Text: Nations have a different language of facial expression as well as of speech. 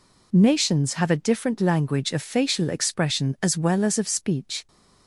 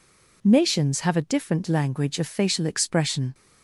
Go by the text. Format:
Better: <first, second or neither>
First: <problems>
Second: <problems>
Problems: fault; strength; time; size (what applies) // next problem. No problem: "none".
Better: first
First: none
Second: stops before "as well as of speech"; at 3.3 s